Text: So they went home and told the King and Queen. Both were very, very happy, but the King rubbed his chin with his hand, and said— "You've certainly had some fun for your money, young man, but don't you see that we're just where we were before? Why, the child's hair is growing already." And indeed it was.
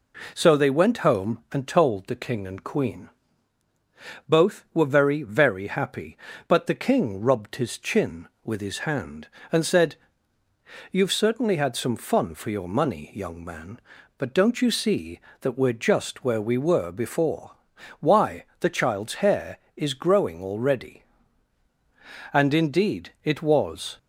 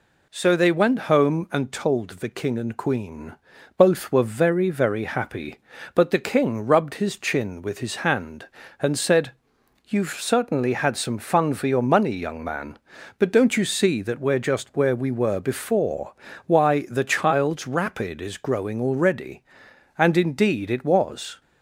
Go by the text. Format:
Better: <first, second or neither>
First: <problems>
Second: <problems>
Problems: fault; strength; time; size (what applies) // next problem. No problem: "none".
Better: first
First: none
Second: says "rapid" for "hair"; at 17.6 s